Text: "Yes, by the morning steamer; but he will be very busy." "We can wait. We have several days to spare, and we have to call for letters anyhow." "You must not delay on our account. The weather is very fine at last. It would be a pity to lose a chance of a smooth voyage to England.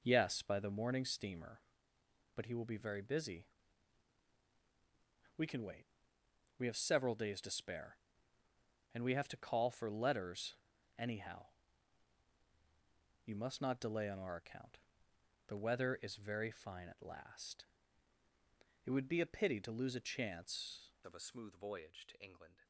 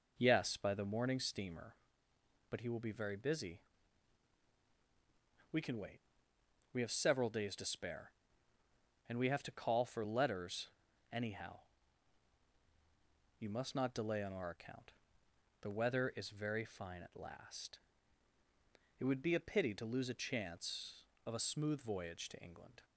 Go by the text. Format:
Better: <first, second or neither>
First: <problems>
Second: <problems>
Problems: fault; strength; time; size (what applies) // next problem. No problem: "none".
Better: second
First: pauses between "letters" and "anyhow"; at 10.5 s; 0.42 s long // changes voice at "of"; from 21.0 s on; 1.6 s long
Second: pauses between "letters" and "anyhow"; at 10.7 s; 0.42 s long